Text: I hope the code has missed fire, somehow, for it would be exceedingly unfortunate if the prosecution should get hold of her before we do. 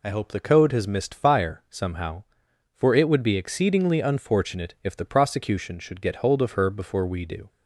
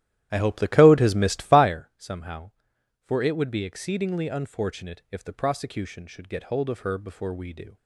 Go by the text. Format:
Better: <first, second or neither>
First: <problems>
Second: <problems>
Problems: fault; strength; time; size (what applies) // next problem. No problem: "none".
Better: first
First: none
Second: starts louder than the rest; strong; until 1.7 s; 12.5 dB